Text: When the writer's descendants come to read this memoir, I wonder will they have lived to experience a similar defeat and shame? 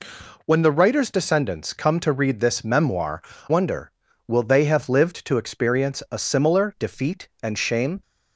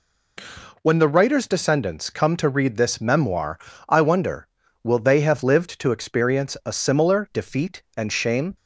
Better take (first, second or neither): second